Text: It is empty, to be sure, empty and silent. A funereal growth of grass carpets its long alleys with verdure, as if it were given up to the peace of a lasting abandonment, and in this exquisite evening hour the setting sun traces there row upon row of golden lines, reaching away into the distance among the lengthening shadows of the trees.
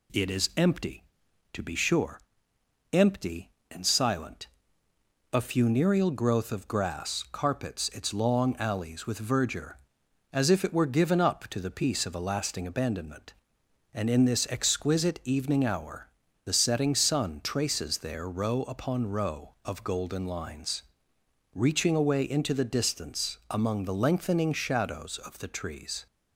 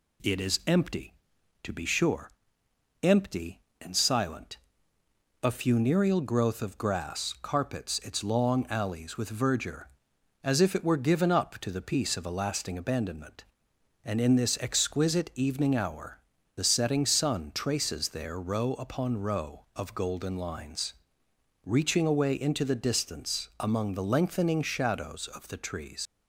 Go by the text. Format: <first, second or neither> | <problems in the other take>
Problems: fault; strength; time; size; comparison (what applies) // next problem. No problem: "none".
first | pauses between "hour" and "the"; slight; at 16.1 s; 0.36 s long; slight in the first // leaves "trees" unfinished; at 26.0 s; 100 ms